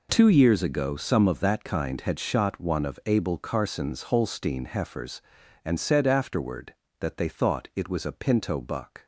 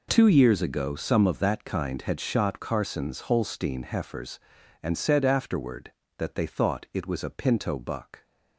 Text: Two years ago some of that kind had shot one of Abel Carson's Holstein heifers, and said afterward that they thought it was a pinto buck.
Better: first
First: none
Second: skips "one of Abel"; at 2.5 s

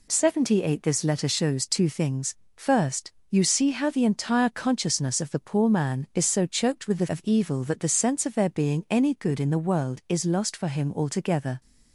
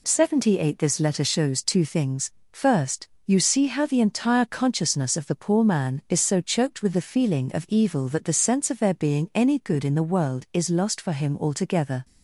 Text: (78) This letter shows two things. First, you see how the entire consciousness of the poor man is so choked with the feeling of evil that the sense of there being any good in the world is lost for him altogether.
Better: second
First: skips "feeling"; at 7.0 s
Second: none

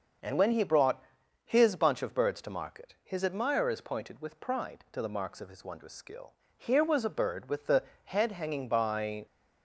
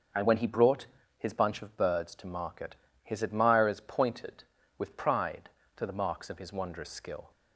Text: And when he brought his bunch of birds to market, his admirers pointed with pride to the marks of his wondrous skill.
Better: second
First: starts louder than the rest; noticeable; until 1.6 s; 6 dB // pauses between "brought" and "his"; at 1.0 s; 0.42 s long // goes on to say "Here was a bird with the head hanging by"; strong; from 6.5 s on; 2.7 s long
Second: starts louder than the rest; until 1.4 s; 6.5 dB // pauses between "brought" and "his"; slight; at 0.8 s; 0.32 s long

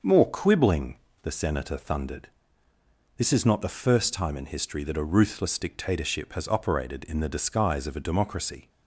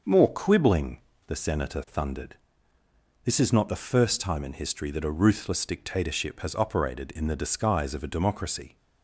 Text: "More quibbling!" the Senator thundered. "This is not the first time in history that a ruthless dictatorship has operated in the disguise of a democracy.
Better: neither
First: starts louder than the rest; noticeable; until 1.2 s; 6 dB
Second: starts louder than the rest; noticeable; until 1.3 s; 6 dB

